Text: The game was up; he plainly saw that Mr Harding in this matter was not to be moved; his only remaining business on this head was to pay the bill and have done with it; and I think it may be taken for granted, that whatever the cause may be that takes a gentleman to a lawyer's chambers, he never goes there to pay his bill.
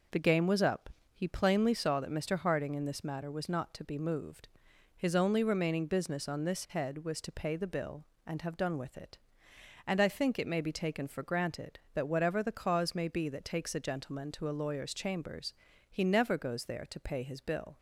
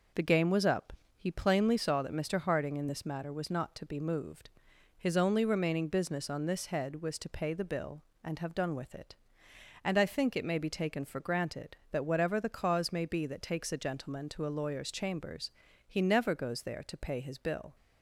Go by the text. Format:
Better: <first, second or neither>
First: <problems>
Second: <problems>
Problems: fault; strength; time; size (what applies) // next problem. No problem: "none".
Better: neither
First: none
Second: none